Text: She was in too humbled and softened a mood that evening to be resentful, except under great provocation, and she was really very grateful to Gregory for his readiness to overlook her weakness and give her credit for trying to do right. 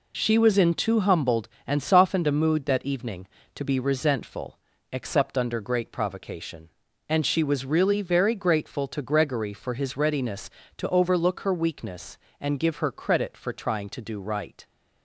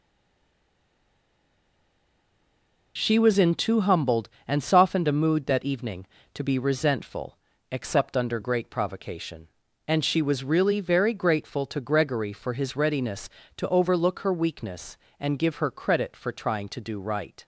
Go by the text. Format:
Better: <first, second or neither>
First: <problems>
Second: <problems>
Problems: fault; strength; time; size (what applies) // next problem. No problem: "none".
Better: first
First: none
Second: stays silent before the first word; strong; until 2.9 s; 2.9 s long